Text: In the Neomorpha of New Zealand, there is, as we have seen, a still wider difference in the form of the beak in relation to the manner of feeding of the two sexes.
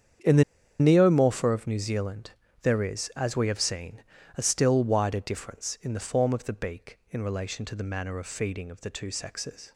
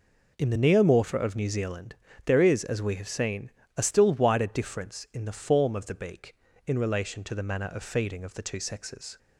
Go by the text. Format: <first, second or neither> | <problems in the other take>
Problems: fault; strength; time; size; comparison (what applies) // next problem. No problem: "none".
second | starts louder than the rest; strong; until 1.6 s; 8 dB // pauses between "the" and "Neomorpha"; at 0.4 s; 0.37 s long